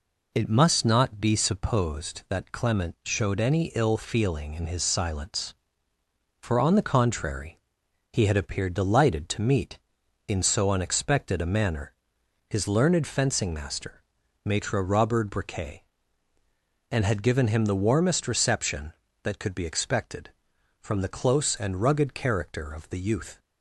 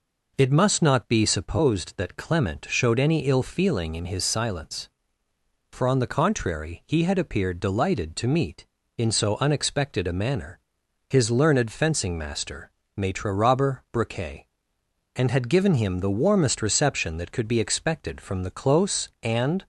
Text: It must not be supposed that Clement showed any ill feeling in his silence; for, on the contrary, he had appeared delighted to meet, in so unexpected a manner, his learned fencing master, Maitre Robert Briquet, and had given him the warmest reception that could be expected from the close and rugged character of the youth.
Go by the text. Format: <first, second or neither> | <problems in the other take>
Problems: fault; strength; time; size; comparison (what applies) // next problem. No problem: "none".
first | stops before "rugged character of the youth"; at 19.6 s